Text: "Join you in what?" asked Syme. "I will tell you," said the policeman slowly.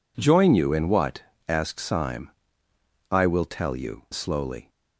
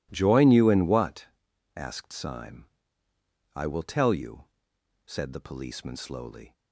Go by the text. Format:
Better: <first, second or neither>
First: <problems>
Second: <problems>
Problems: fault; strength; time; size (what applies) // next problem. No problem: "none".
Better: second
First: skips "said the policeman"; at 4.0 s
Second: none